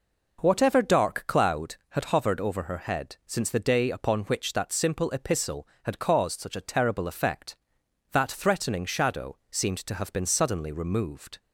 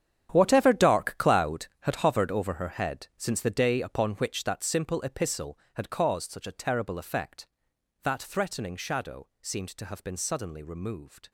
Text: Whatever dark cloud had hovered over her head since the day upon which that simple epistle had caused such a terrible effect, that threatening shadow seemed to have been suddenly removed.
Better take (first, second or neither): first